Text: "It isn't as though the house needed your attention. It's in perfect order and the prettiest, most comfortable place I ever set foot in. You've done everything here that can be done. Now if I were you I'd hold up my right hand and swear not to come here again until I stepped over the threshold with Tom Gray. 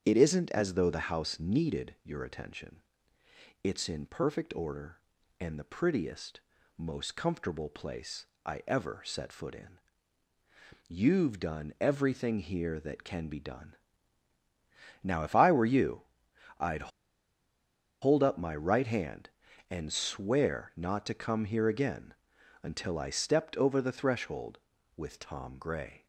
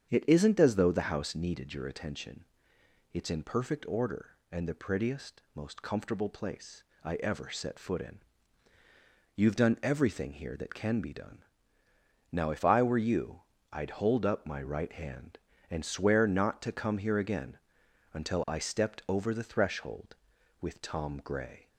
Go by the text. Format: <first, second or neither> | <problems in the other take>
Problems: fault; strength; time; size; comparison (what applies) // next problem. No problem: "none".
second | starts louder than the rest; strong; until 1.0 s; 7.5 dB; strong in the second // pauses between "place" and "I"; slight; at 8.2 s; 0.18 s long; slight in the second // pauses between "you" and "I'd"; noticeable; at 16.0 s; 0.58 s long; slight in the second // pauses between "I'd" and "hold"; at 16.9 s; 1.1 s long // pauses between "again" and "until"; noticeable; at 22.1 s; 0.48 s long; noticeable in the second